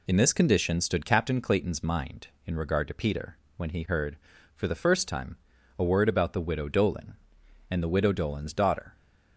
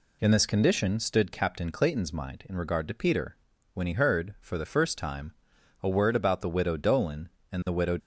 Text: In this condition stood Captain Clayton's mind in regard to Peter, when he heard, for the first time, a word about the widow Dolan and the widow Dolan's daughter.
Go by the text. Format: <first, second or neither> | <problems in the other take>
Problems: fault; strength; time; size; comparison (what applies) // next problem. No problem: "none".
first | stops before "Dolan's daughter"; at 8.0 s